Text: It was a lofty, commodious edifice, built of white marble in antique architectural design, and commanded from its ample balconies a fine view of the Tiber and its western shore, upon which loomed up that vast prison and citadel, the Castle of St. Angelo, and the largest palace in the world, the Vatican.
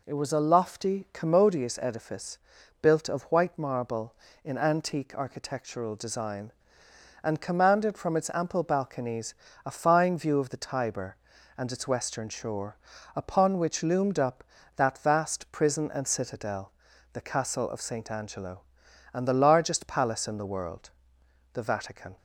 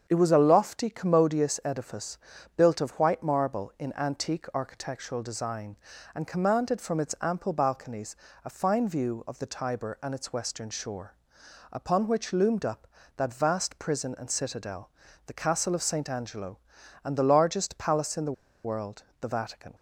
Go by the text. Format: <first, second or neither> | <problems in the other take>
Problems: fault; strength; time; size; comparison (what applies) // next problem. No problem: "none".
first | starts louder than the rest; strong; until 1.0 s; 7.5 dB // pauses between "balconies" and "a"; slight; at 8.1 s; 0.26 s long; slight in the first // pauses between "the" and "world"; slight; at 18.3 s; 0.32 s long